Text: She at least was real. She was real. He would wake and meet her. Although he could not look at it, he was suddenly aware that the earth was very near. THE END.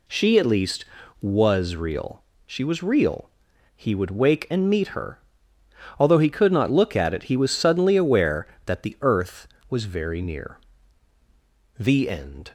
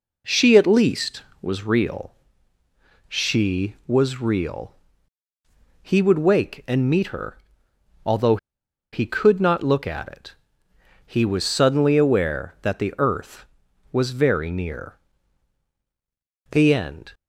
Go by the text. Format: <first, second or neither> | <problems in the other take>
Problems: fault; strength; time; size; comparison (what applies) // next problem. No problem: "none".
first | pauses between "Although" and "he"; noticeable; at 8.3 s; 0.56 s long